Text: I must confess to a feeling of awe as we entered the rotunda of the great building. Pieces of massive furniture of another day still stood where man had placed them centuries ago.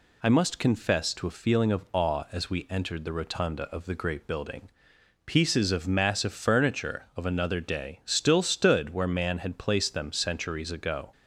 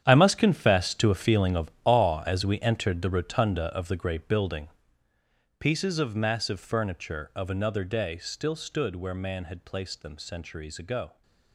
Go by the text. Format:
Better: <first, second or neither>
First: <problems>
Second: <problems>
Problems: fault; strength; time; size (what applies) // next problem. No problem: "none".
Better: first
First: none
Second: gets quieter; strong; throughout; 13.5 dB